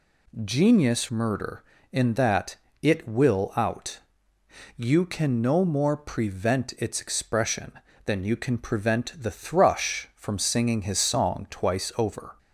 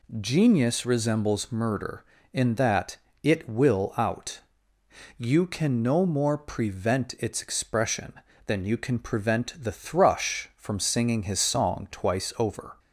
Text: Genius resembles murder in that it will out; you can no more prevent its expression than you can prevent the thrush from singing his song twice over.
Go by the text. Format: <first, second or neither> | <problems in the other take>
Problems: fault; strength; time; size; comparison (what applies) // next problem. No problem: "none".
second | skips "resembles"; at 1.0 s // pauses between "that" and "it"; slight; at 2.5 s; 0.26 s long; slight in the second